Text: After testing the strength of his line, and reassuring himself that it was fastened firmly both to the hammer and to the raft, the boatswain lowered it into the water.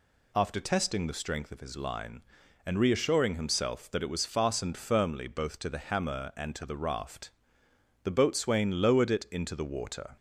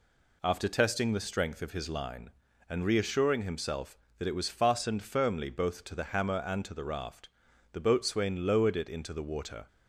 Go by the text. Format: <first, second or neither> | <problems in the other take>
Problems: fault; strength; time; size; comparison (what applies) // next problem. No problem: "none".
neither | none